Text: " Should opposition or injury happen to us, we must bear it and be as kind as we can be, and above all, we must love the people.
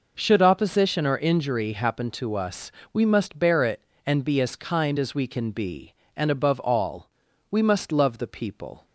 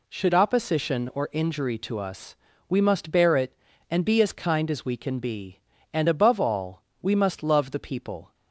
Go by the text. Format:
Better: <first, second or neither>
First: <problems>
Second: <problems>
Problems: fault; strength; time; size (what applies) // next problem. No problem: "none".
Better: first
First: none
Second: skips "happen"; at 1.7 s